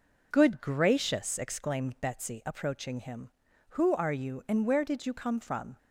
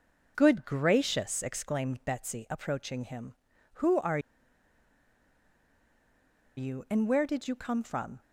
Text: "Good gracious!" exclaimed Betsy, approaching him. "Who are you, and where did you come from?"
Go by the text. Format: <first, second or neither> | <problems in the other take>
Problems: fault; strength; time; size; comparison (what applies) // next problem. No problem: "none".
first | pauses between "are" and "you"; strong; at 4.1 s; 2.3 s long